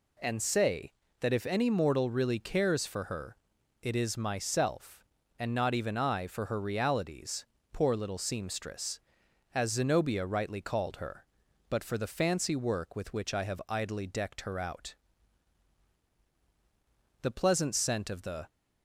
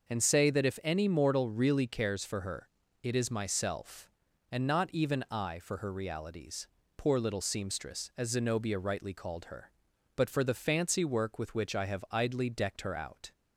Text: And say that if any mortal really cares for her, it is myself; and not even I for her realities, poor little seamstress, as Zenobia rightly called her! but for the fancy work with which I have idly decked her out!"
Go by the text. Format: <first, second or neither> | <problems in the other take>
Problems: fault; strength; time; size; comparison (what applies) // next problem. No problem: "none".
second | goes on to say "The pleasant scent of the"; noticeable; from 17.1 s on; 1.2 s long